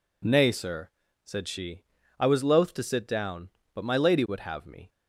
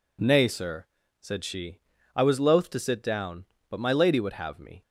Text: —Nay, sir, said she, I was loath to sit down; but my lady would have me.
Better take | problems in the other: neither | none

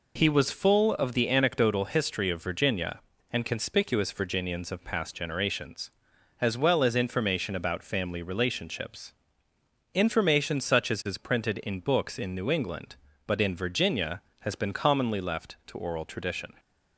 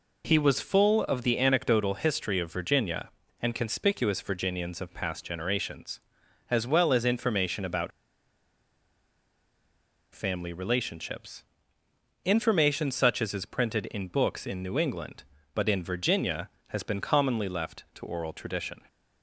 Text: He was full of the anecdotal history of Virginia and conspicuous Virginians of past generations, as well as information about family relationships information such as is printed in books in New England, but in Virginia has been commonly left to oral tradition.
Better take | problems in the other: first | pauses between "about" and "family"; strong; at 7.9 s; 2.2 s long // pauses between "relationships" and "information"; noticeable; at 11.4 s; 0.80 s long; noticeable in the first

